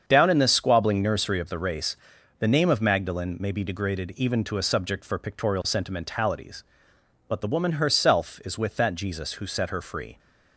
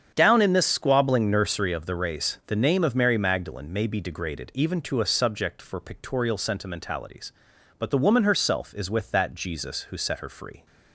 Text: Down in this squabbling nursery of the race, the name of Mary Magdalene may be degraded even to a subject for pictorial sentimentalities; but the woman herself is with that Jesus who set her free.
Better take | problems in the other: second | starts louder than the rest; strong; until 1.0 s; 7.5 dB; strong in the second // skips "Mary"; at 2.8 s

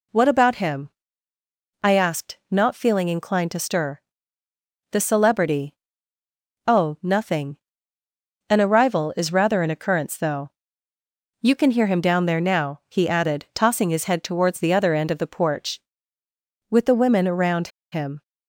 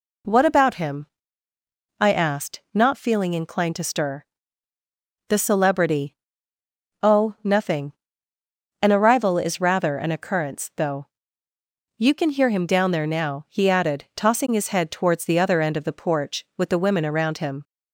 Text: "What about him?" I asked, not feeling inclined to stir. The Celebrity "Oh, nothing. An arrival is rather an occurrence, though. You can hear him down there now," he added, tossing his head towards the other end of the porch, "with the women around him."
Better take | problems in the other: second | pauses between "Celebrity" and "Oh"; noticeable; at 5.7 s; 0.92 s long; noticeable in the second // pauses between "around" and "him"; slight; at 17.6 s; 0.23 s long

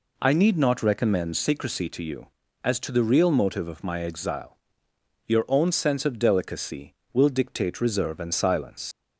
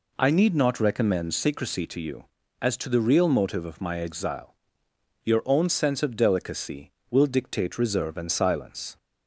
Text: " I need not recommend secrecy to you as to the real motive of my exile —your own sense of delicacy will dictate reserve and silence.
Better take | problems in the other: second | leaves "silence" unfinished; at 8.9 s; 80 ms

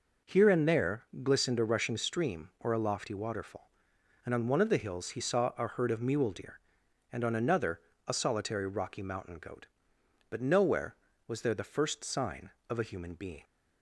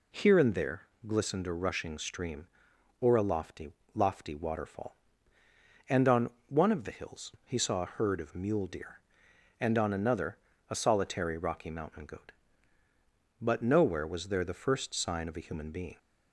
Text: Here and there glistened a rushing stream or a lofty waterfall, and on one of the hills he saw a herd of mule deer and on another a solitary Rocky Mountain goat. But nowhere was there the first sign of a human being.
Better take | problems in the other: first | pauses between "there" and "glistened"; slight; at 0.8 s; 0.24 s long; slight in the first // says "lofty" twice; at 3.9 s // pauses between "on" and "one"; slight; at 6.2 s; 0.20 s long // pauses between "another" and "a"; slight; at 10.3 s; 0.32 s long; slight in the first

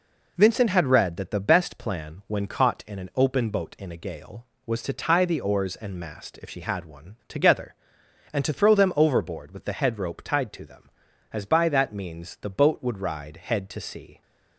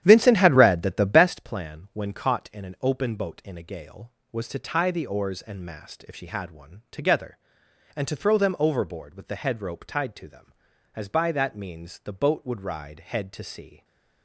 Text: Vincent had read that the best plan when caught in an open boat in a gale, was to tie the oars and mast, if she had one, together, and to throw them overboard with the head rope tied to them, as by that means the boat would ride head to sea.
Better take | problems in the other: first | starts louder than the rest; strong; until 1.4 s; 10.5 dB // stays silent after the last word; slight; from 13.7 s on; 0.5 s long

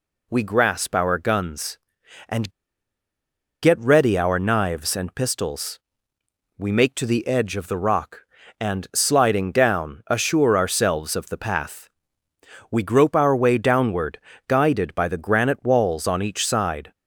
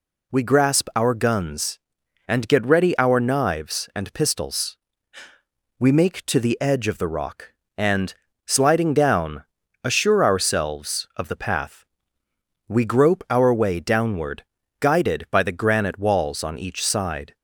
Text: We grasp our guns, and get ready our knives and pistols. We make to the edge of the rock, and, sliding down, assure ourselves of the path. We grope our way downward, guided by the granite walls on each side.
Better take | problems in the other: second | pauses between "and" and "get"; at 2.5 s; 1.1 s long

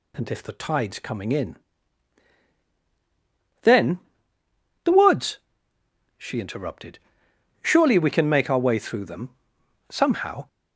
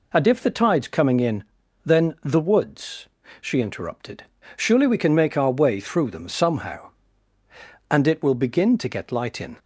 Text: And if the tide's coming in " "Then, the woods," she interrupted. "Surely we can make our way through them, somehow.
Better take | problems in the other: first | goes on to say "And it will begin to get light in"; strong; from 7.9 s on; 1.6 s long

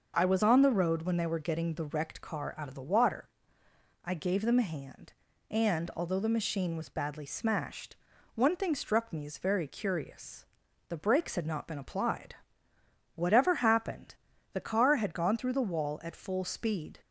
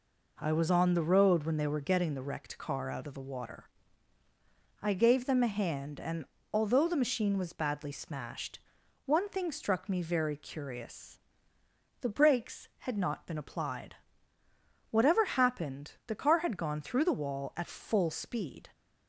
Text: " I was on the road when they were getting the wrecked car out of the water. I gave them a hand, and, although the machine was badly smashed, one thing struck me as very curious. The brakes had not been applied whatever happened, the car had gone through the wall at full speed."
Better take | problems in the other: first | skips "as"; at 10.0 s // pauses between "applied" and "whatever"; noticeable; at 13.9 s; 0.94 s long; noticeable in the first

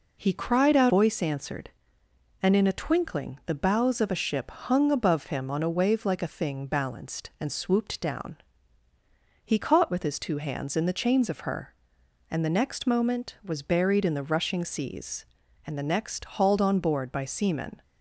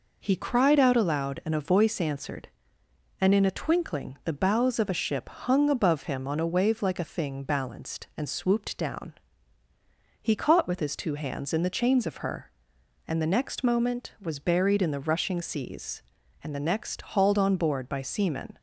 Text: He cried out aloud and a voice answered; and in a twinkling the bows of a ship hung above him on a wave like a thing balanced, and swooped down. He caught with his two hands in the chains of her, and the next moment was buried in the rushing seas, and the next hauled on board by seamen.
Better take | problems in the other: second | skips "aloud and a"; at 0.9 s

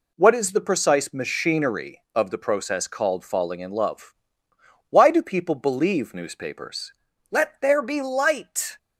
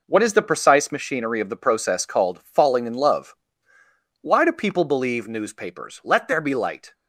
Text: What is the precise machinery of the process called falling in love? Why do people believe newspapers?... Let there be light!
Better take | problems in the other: neither | none

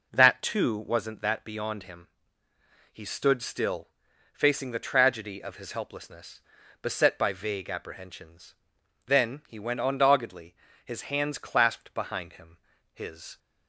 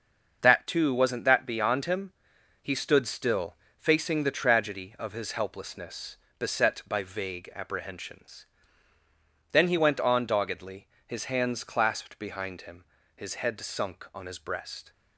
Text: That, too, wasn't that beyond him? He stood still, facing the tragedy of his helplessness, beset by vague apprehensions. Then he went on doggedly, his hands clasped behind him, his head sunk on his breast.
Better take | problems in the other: second | stops before "head sunk on his breast"; at 13.3 s

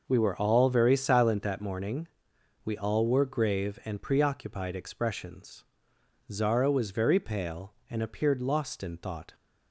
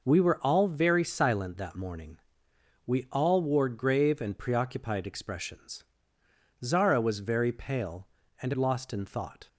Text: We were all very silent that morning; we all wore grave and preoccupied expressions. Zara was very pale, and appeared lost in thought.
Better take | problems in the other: first | skips "appeared"; at 8.5 s

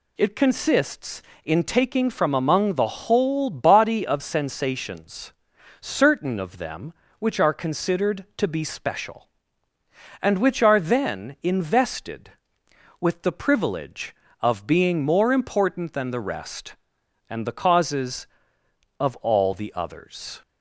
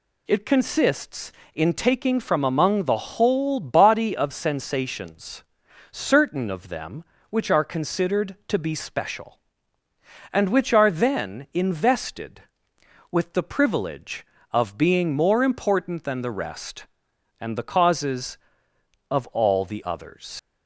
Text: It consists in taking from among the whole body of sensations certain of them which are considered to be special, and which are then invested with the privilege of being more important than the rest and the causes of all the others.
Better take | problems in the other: first | pauses between "sensations" and "certain"; noticeable; at 5.4 s; 0.50 s long; noticeable in the first // leaves "others" unfinished; at 20.3 s; 115 ms

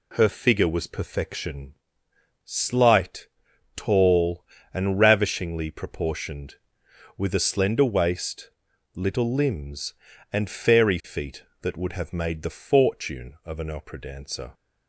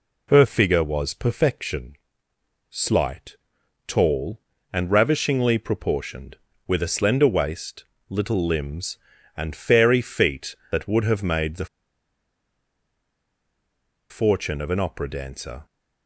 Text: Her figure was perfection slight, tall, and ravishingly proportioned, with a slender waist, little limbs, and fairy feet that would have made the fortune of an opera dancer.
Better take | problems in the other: first | pauses between "perfection" and "slight"; noticeable; at 1.9 s; 0.74 s long; noticeable in the first // pauses between "the" and "fortune"; strong; at 11.6 s; 2.4 s long

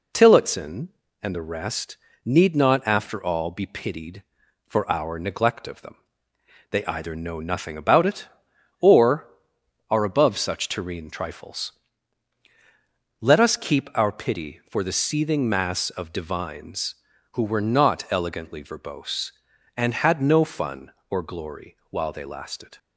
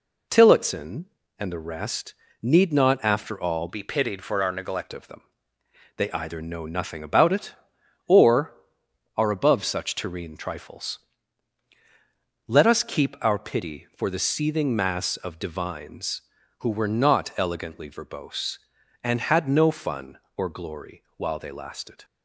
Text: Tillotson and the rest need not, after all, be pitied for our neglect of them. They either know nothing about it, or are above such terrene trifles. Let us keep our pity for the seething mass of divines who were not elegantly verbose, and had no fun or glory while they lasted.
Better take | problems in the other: first | pauses between "rest" and "need"; slight; at 2.1 s; 0.28 s long; slight in the first // changes voice from "be" to "neglect"; from 3.6 to 4.9 s; 1.3 s long

